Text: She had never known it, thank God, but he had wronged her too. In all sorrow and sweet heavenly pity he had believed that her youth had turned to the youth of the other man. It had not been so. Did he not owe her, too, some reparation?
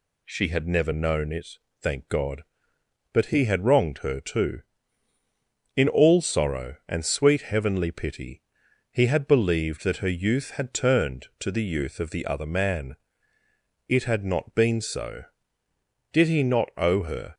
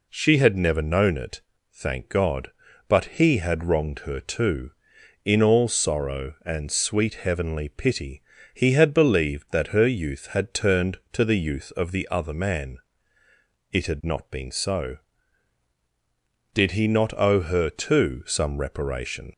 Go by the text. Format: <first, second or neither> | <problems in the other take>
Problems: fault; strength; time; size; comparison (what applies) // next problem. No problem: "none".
second | pauses between "pity" and "he"; noticeable; at 8.4 s; 0.49 s long; slight in the second // stops before "too some reparation"; at 17.3 s